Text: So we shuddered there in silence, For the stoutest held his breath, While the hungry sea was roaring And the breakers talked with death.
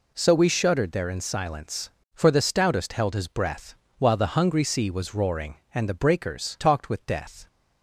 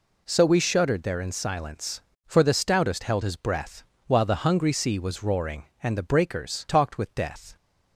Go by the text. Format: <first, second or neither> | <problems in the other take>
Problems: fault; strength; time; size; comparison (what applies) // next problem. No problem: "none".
neither | none